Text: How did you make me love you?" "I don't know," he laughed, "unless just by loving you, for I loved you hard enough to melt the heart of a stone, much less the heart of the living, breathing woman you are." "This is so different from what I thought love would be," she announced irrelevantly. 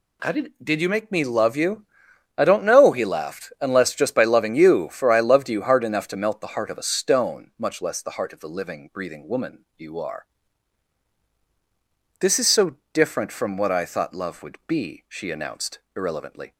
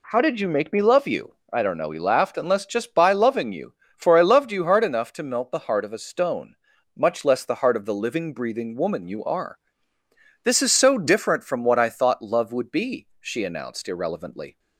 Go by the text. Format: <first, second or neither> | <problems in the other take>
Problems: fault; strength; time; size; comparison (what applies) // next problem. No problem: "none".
second | says "did" twice; at 0.6 s // pauses between "so" and "different"; slight; at 12.7 s; 0.16 s long // pauses between "announced" and "irrelevantly"; slight; at 15.7 s; 0.18 s long